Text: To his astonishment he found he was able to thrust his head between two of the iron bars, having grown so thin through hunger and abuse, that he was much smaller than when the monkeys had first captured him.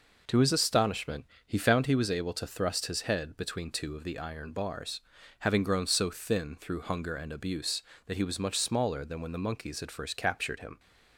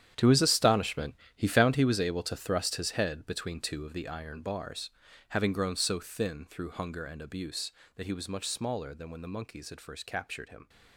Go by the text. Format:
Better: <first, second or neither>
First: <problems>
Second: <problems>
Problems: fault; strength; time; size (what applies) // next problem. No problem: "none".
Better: first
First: pauses between "astonishment" and "he"; slight; at 1.2 s; 0.20 s long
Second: gets quieter; strong; throughout; 14 dB // pauses between "astonishment" and "he"; slight; at 1.1 s; 0.20 s long